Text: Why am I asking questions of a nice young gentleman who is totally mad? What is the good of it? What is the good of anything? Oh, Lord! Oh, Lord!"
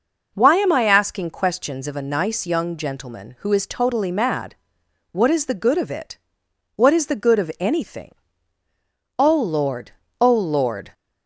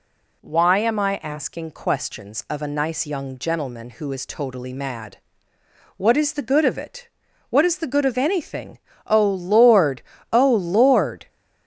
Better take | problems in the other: neither | none

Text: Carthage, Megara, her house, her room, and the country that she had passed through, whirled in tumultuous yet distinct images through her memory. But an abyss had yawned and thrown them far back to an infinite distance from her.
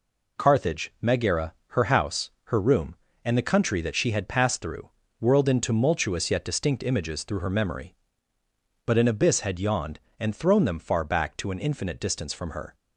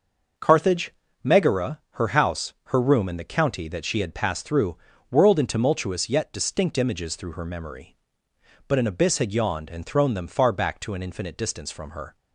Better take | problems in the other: first | says "county" for "country"; at 3.2 s

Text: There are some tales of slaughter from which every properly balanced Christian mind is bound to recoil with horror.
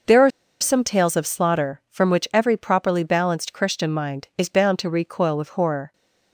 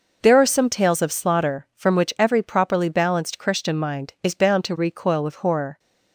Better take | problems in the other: second | pauses between "are" and "some"; slight; at 0.3 s; 0.30 s long

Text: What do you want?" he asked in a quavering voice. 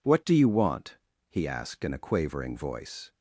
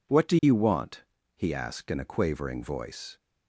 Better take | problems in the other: neither | none

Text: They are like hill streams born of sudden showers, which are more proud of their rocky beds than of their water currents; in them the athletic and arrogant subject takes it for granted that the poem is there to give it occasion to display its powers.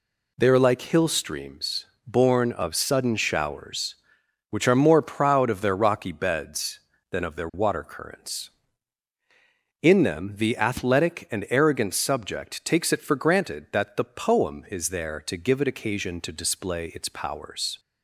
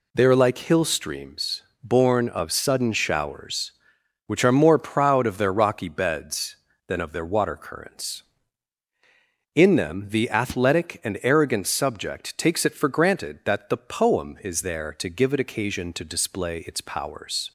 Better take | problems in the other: neither | pauses between "streams" and "born"; slight; the same in both

